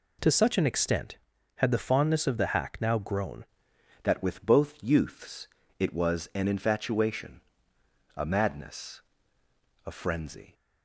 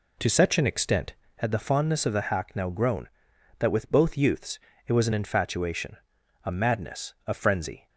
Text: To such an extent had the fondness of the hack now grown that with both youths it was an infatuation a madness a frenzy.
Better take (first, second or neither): second